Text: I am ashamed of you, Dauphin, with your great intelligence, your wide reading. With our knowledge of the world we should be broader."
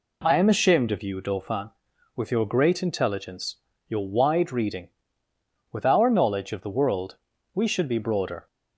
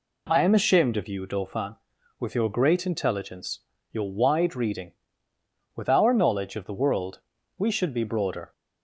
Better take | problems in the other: neither | pauses between "world" and "we"; the same in both

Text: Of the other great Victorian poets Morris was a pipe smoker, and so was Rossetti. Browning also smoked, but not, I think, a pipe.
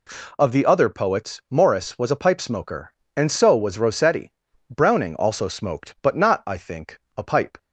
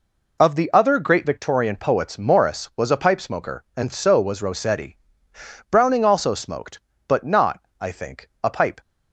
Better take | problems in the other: second | skips "great Victorian"; at 0.8 s

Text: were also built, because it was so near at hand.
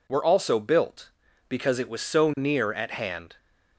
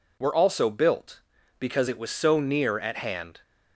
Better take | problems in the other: neither | none

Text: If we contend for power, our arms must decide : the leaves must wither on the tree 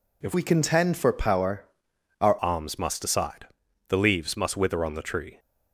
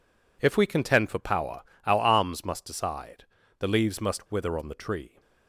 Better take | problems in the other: second | changes voice from "we" to "our"; from 0.3 to 2.3 s; 2.0 s long

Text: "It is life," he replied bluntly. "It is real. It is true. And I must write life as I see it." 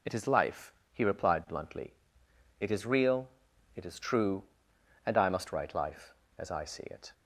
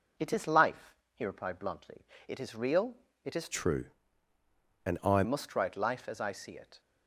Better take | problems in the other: first | changes voice from "true" to "I"; from 3.5 to 5.2 s; 1.7 s long

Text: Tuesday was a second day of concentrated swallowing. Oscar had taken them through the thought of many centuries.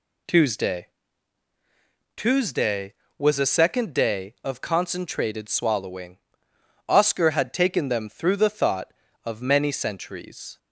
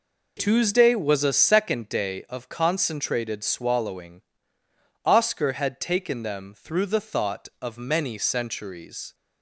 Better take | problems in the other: second | says "Tuesday" twice; at 2.1 s

